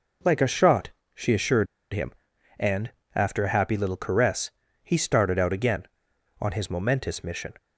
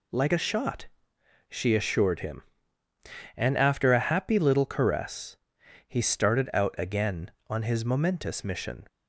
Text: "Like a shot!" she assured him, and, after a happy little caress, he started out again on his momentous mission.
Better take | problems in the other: second | pauses between "assured" and "him"; slight; at 1.6 s; 0.26 s long

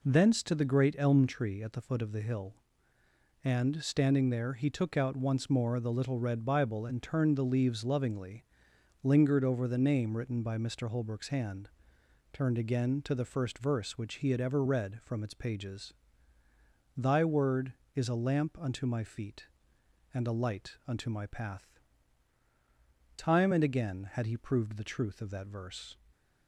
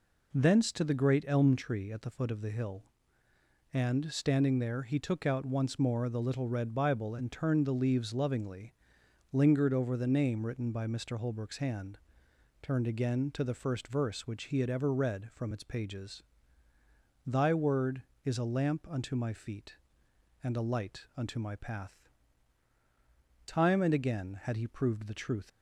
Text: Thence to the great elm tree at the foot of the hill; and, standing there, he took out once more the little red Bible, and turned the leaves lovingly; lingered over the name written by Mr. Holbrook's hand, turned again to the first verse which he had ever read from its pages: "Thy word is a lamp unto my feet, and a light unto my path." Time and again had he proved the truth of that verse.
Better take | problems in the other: first | stops before "of that verse"; at 25.4 s

